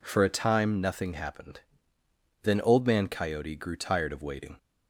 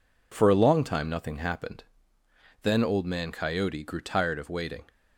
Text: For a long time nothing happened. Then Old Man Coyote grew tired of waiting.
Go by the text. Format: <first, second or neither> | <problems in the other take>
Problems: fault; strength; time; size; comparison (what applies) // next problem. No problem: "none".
second | skips "long"; at 0.2 s